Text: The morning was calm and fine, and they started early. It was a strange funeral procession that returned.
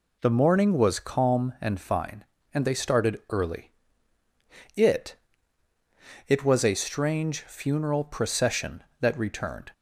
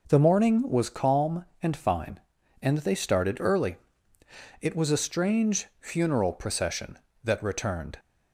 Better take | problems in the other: second | says "It" twice; at 6.2 s

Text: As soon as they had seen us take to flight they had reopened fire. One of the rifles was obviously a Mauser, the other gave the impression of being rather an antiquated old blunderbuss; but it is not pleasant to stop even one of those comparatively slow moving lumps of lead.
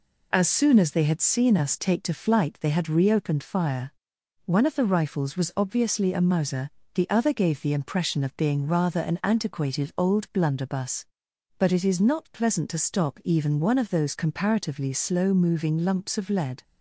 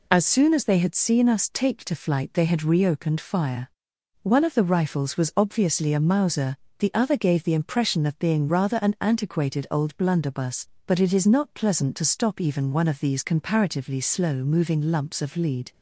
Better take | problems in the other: first | says "these" for "those"; at 12.9 s

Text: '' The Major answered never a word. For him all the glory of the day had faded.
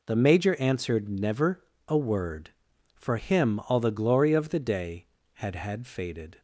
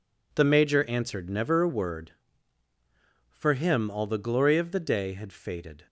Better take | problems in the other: second | pauses between "never" and "a"; slight; at 1.6 s; 0.24 s long // says "had" twice; at 5.5 s

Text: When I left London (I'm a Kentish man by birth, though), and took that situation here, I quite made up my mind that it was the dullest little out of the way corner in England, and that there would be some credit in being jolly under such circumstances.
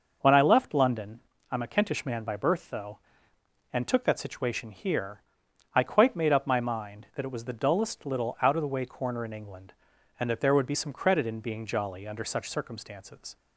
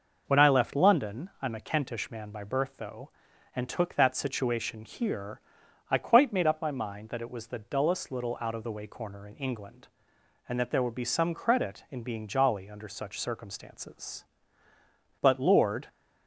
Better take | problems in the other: first | goes on to say "But Lord"; noticeable; from 15.2 s on; 0.66 s long

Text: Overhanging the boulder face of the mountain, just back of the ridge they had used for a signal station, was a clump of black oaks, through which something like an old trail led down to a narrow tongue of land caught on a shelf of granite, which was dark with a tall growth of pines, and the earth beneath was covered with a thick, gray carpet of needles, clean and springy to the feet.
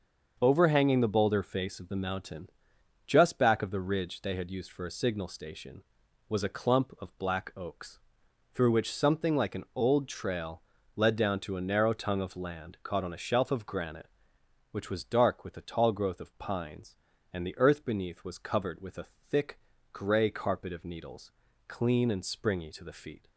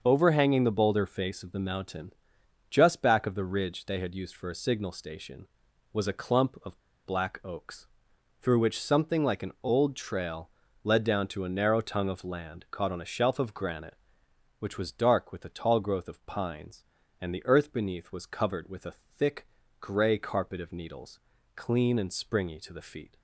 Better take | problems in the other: first | starts louder than the rest; until 1.0 s; 6 dB; also in the first // pauses between "of" and "black"; slight; at 6.8 s; 0.24 s long // pauses between "trail" and "led"; slight; at 10.4 s; 0.34 s long; slight in the first // pauses between "a" and "thick"; slight; at 18.9 s; 0.24 s long; slight in the first

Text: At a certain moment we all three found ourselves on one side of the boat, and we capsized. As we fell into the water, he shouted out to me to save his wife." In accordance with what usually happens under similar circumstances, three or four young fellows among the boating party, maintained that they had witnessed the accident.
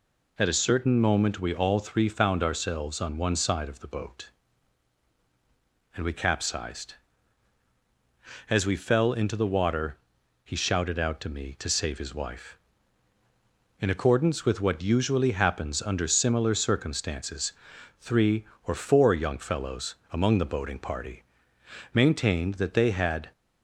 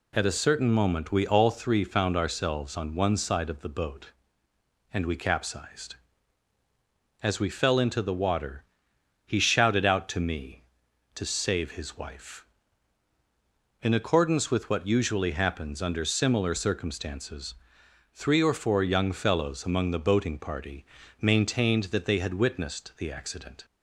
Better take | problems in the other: second | pauses between "fellows" and "among"; slight; at 19.9 s; 0.16 s long // stops before "witnessed the accident"; at 23.3 s

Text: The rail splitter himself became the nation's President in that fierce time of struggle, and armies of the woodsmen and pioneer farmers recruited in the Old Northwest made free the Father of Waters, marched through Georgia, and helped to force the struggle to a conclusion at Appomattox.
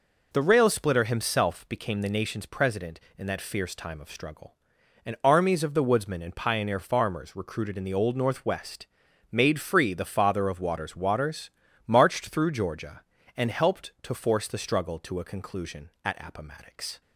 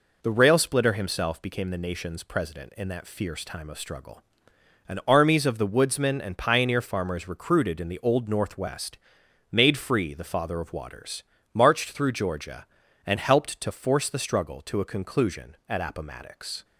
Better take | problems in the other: second | pauses between "Northwest" and "made"; at 8.8 s; 0.44 s long; noticeable in the second // says "Waters" twice; at 10.9 s

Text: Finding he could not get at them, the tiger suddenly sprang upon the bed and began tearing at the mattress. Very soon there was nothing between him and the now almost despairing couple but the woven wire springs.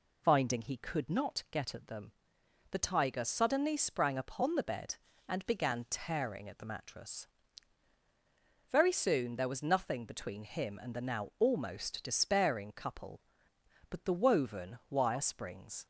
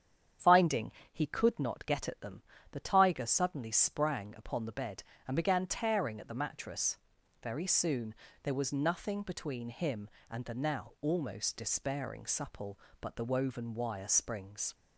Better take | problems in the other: first | starts louder than the rest; strong; until 1.6 s; 8.5 dB // pauses between "Finding" and "he"; slight; at 0.9 s; 0.22 s long // pauses between "soon" and "there"; slight; at 8.1 s; 0.30 s long // says "supple" for "couple"; at 12.2 s

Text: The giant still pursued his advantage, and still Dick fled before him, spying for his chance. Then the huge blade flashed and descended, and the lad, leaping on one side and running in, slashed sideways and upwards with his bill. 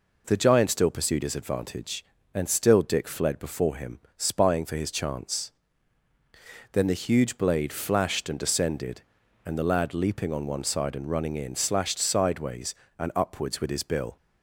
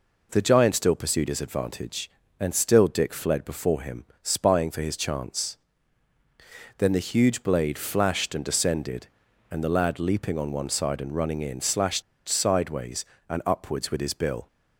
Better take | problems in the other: first | pauses between "slashed" and "sideways"; slight; at 12.0 s; 0.25 s long

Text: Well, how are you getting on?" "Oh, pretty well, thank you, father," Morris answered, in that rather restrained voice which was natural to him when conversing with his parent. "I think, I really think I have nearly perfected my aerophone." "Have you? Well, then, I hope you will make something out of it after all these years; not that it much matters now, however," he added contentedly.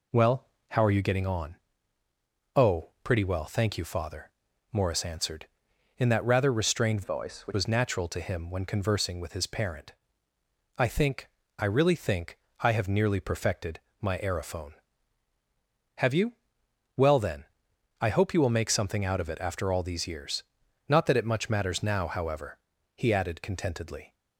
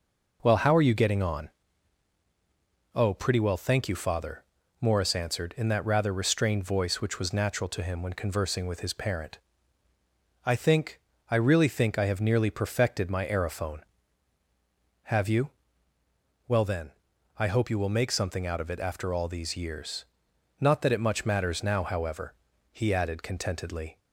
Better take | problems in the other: second | changes voice from "voice" to "which"; from 7.0 to 7.5 s; 0.5 s long // pauses between "think" and "I"; slight; at 12.3 s; 0.24 s long // pauses between "perfected" and "my"; slight; at 13.7 s; 0.22 s long

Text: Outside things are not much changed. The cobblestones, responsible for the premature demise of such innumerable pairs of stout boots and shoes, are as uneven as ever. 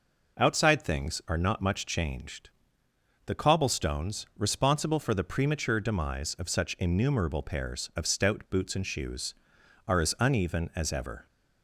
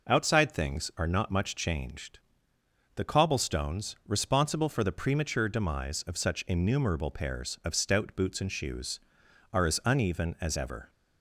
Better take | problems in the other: neither | none

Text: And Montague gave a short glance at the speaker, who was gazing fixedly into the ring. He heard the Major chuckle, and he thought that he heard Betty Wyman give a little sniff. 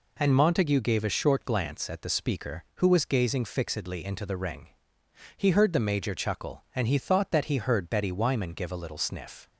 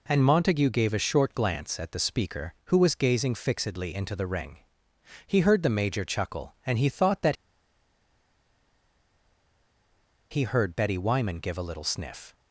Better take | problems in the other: first | pauses between "that" and "he"; strong; at 7.3 s; 2.9 s long

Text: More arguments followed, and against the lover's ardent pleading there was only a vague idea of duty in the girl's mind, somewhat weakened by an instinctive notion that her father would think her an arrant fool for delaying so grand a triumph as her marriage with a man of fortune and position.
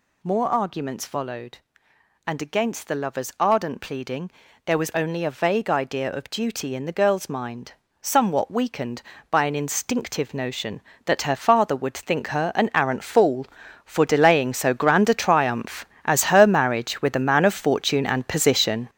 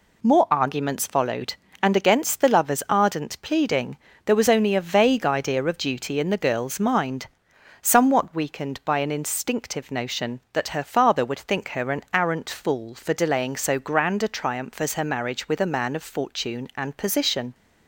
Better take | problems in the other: second | gets louder; strong; throughout; 8.5 dB // pauses between "pleading" and "there"; slight; at 4.3 s; 0.34 s long; slight in the second

